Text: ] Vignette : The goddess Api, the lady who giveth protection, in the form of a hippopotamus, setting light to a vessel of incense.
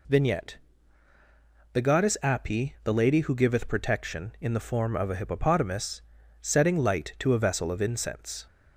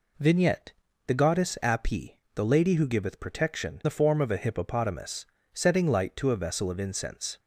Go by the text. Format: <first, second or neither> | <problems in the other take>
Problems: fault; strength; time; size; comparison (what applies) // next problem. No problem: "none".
first | skips "in"; at 3.8 s